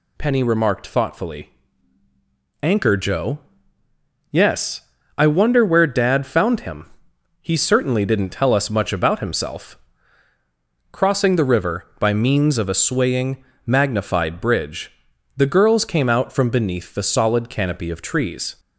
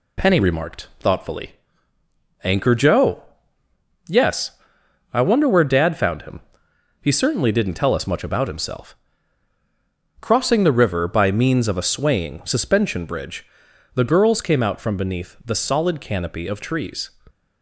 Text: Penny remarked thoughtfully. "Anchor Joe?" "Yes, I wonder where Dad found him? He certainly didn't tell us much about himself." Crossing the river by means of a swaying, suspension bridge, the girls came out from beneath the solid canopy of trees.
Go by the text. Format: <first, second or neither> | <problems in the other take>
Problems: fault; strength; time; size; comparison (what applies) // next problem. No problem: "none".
second | says "magnified" for "suspension"; at 13.6 s